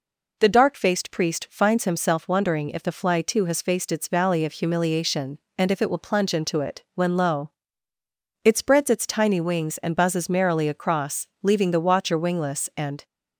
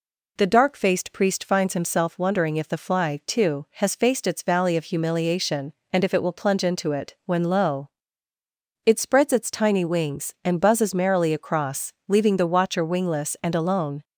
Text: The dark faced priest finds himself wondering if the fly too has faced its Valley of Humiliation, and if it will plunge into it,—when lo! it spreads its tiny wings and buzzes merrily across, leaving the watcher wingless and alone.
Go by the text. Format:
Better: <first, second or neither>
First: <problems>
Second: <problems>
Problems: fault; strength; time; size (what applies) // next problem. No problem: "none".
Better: second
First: stops before "alone"; at 13.0 s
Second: none